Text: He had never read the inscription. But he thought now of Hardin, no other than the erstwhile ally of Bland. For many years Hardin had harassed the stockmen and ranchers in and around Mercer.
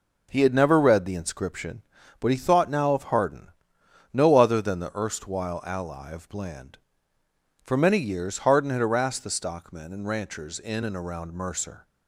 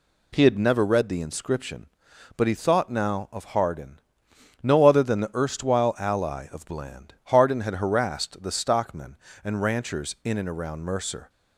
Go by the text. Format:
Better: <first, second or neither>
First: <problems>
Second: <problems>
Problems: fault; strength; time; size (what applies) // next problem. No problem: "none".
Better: first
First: none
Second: skips "For many years"; at 7.1 s